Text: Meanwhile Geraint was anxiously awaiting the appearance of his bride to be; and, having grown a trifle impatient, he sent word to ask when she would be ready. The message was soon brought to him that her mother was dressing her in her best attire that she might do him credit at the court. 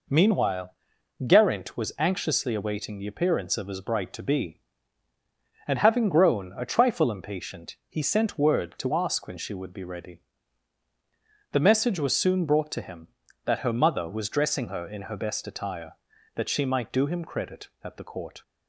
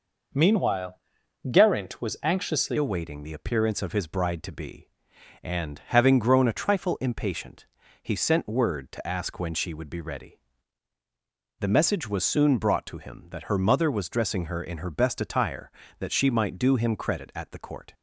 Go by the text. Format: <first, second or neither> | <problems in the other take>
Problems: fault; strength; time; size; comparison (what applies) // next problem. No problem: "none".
first | pauses between "Meanwhile" and "Geraint"; noticeable; at 0.9 s; 0.52 s long; noticeable in the first // changes voice at "awaiting"; from 2.7 s on; 15.2 s long